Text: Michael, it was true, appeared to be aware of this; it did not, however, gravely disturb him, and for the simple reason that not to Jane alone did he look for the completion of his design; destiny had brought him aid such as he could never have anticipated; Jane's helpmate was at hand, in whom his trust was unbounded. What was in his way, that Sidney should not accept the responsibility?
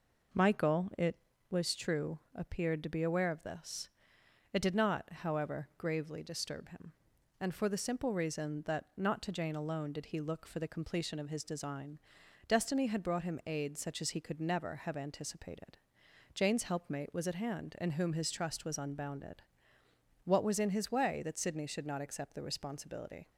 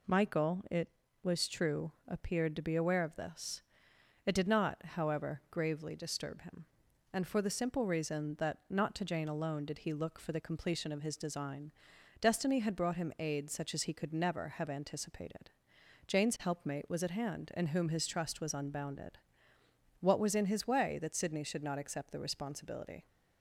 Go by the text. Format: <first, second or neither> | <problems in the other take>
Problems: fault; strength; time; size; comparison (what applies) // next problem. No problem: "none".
second | starts louder than the rest; noticeable; until 1.6 s; 5 dB